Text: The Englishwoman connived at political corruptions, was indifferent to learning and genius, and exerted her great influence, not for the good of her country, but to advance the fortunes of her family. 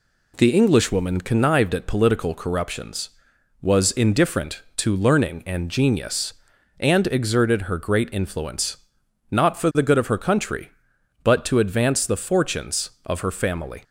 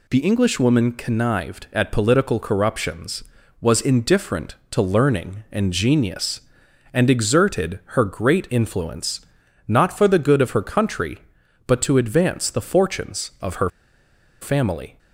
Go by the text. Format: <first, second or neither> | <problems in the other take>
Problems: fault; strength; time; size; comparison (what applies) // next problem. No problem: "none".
first | pauses between "exerted" and "her"; slight; at 7.7 s; 0.18 s long // pauses between "her" and "family"; noticeable; at 13.6 s; 0.72 s long